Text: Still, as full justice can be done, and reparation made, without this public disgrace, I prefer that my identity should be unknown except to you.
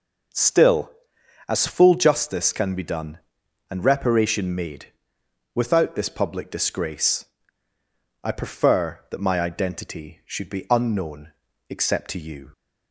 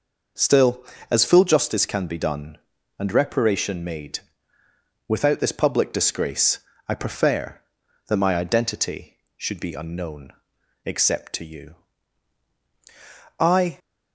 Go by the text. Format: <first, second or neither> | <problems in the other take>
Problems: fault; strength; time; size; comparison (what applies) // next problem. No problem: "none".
first | pauses between "unknown" and "except"; at 10.3 s; 0.44 s long; slight in the first // goes on to say "I"; slight; from 13.4 s on; 0.38 s long